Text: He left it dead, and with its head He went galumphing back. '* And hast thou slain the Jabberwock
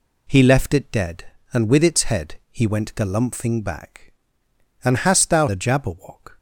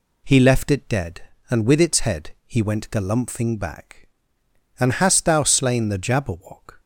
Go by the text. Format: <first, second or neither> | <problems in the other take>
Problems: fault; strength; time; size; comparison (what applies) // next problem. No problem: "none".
second | skips "slain"; at 5.4 s